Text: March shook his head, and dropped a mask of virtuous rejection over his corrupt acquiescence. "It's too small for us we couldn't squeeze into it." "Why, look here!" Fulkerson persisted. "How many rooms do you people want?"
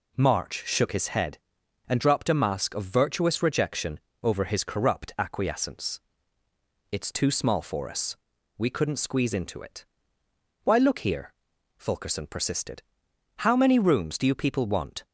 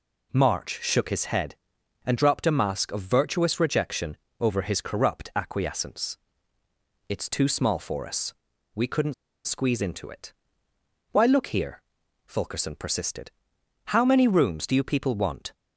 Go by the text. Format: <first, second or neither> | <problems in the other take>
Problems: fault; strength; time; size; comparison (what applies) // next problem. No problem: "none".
first | pauses between "rejection" and "over"; slight; at 4.1 s; 0.24 s long; slight in the first // pauses between "us" and "we"; at 8.3 s; 0.42 s long; also in the first // pauses between "couldn't" and "squeeze"; slight; at 9.1 s; 0.33 s long